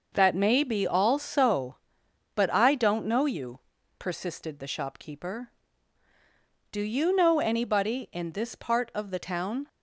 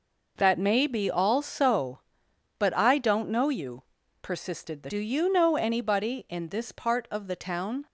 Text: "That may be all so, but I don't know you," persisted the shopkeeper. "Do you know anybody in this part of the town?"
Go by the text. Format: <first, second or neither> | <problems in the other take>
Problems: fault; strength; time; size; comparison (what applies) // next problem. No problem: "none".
first | skips "shopkeeper"; at 4.8 s